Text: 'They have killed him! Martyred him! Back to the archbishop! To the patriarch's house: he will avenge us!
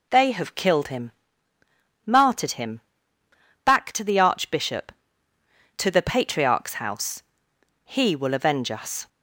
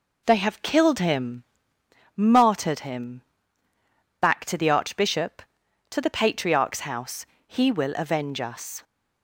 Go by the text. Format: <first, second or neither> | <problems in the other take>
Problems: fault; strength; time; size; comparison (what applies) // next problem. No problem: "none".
first | starts louder than the rest; noticeable; until 2.1 s; 4.5 dB